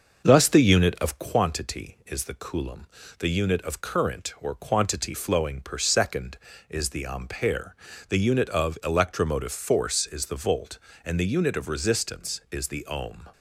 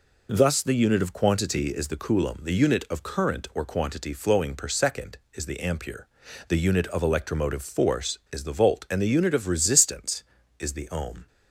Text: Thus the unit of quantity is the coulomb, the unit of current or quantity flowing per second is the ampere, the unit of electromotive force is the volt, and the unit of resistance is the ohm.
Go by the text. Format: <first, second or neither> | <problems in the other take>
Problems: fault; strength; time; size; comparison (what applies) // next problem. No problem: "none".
second | starts louder than the rest; until 1.5 s; 6 dB